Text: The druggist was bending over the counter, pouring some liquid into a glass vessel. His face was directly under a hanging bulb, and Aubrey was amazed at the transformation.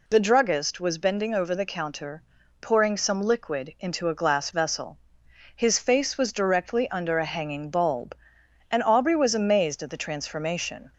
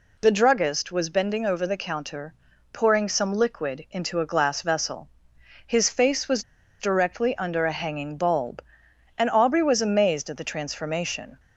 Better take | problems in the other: first | pauses between "was" and "directly"; at 6.4 s; 0.38 s long

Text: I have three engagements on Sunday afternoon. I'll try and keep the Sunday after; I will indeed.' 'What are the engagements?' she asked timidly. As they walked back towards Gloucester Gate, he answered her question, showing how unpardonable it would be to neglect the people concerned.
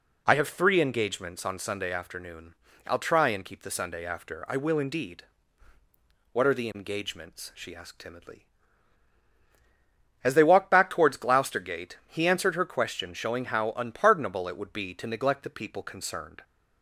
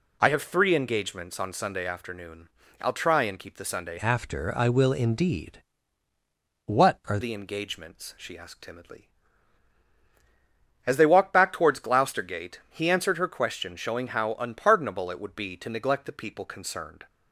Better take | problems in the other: first | changes voice from "after" to "are"; from 3.9 to 7.1 s; 3.2 s long

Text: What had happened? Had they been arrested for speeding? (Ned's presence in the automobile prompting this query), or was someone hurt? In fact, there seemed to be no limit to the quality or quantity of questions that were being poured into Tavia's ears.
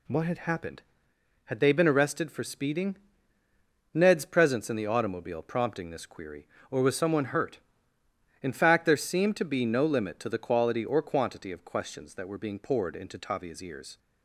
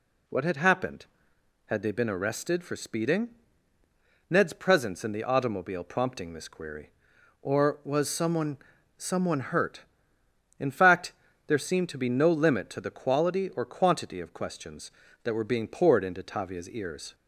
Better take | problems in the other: first | says "someone" twice; at 8.9 s

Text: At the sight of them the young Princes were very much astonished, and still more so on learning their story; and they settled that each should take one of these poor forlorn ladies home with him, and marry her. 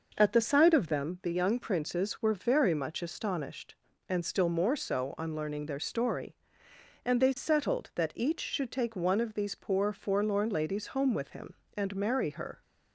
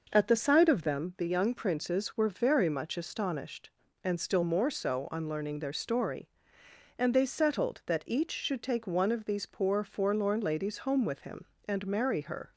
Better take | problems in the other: neither | none

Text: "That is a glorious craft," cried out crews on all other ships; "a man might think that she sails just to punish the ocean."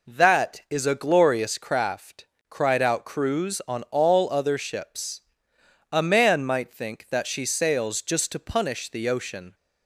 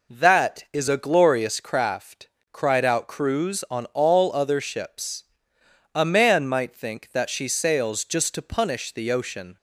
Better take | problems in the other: neither | none

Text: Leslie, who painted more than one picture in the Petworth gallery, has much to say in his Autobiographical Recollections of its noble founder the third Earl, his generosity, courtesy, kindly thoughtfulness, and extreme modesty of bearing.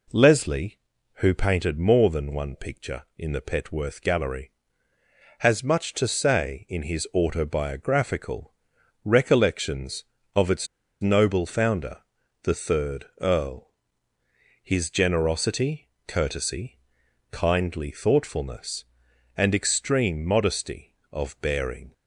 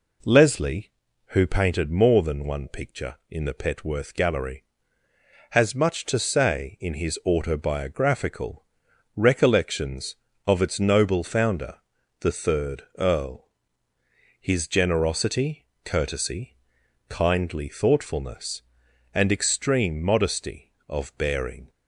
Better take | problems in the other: second | pauses between "Autobiographical" and "Recollections"; noticeable; at 8.5 s; 0.52 s long; noticeable in the second // pauses between "its" and "noble"; slight; at 10.6 s; 0.34 s long // pauses between "founder" and "the"; at 11.9 s; 0.44 s long; also in the second // pauses between "third" and "Earl"; slight; at 13.0 s; 0.16 s long; slight in the second

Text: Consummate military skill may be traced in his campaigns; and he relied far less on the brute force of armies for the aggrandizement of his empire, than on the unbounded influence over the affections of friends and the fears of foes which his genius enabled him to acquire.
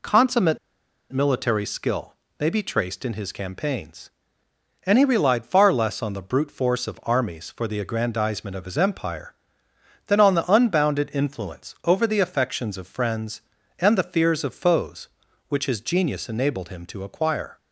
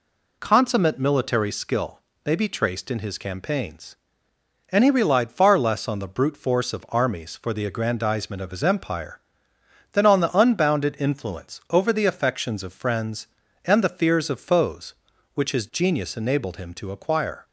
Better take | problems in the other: second | pauses between "Consummate" and "military"; noticeable; at 0.5 s; 0.53 s long // pauses between "skill" and "may"; slight; at 2.1 s; 0.26 s long; slight in the second

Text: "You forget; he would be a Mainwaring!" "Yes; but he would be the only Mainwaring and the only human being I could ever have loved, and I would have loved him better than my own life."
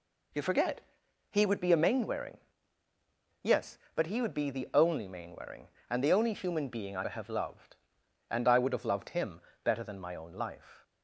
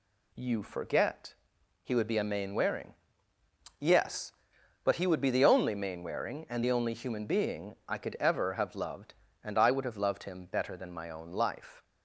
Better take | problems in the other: second | skips "could ever"; at 7.0 s // pauses between "him" and "better"; slight; at 9.3 s; 0.24 s long

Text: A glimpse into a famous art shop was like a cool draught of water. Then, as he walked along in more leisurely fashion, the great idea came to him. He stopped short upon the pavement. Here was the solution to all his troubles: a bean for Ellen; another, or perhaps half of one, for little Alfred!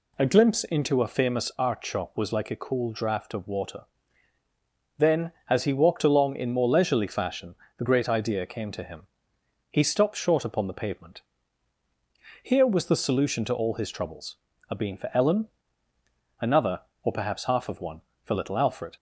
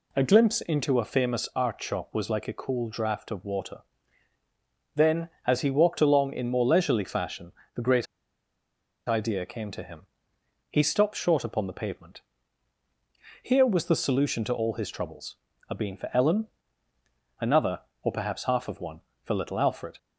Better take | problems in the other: first | pauses between "great" and "idea"; at 8.0 s; 1.0 s long

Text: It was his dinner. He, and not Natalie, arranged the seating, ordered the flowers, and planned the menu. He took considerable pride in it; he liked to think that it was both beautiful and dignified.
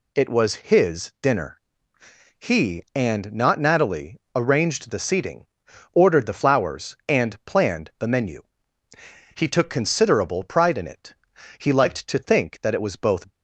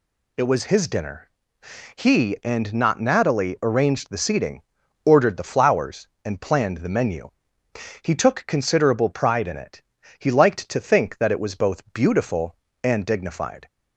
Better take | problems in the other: second | stops before "beautiful and dignified"; at 13.3 s

